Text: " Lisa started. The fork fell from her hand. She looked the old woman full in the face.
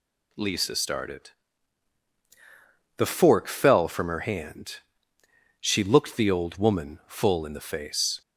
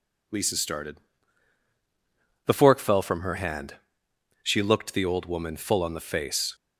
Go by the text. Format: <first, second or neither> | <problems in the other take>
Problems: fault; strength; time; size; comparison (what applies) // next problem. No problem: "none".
first | says "on" for "in"; at 5.8 s